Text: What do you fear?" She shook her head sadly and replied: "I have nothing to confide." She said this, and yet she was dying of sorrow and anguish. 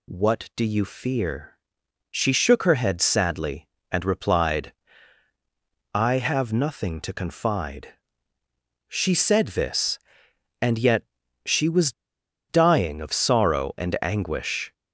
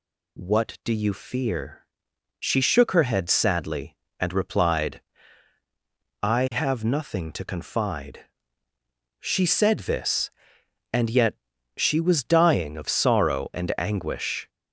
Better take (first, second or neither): second